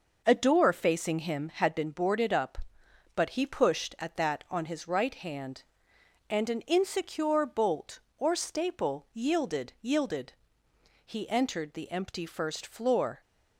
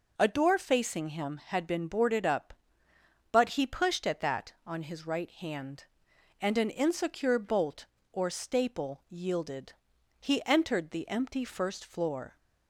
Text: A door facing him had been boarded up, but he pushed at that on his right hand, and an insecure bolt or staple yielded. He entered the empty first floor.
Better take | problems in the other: second | says "yielded" twice; at 9.8 s

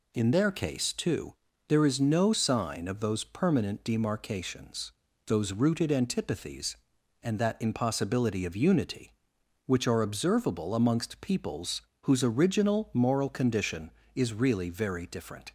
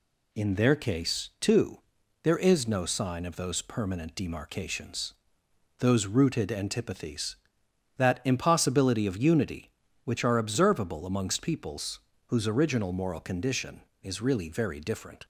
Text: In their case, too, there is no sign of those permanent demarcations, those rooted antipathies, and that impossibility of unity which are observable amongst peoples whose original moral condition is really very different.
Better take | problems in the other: first | skips "and"; at 7.6 s // pauses between "peoples" and "whose"; slight; at 11.9 s; 0.28 s long; slight in the first

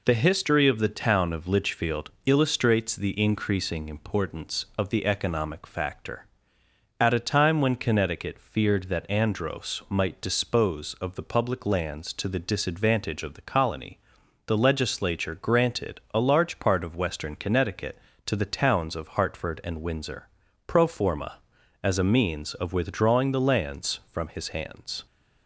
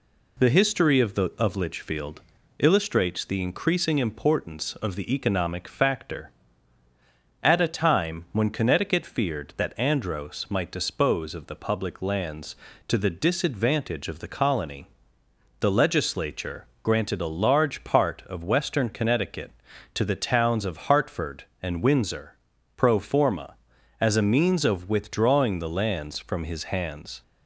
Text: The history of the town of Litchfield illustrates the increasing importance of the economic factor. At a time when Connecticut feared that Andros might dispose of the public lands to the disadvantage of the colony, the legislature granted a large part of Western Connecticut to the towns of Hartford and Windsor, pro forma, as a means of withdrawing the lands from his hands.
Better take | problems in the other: first | skips "town"; at 1.3 s // pauses between "Litchfield" and "illustrates"; at 2.2 s; 0.38 s long // pauses between "legislature" and "granted"; slight; at 16.6 s; 0.18 s long

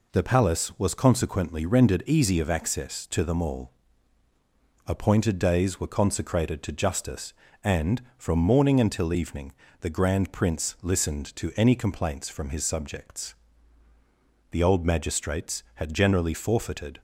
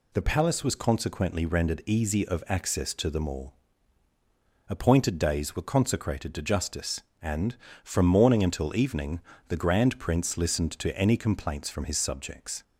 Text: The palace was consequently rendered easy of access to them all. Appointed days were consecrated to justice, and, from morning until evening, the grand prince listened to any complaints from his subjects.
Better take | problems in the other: second | goes on to say "The old magistrates had generally forfeited"; strong; from 14.5 s on; 2.5 s long

